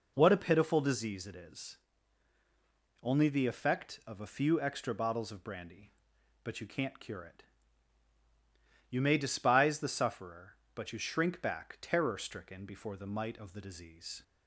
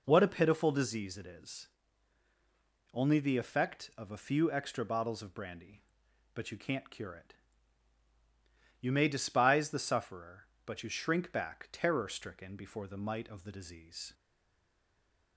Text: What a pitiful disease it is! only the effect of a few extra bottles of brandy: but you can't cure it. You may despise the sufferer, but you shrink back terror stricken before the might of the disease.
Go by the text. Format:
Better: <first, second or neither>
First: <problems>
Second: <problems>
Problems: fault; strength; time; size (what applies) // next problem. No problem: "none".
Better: first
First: none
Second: stays silent after the last word; noticeable; from 14.1 s on; 1.2 s long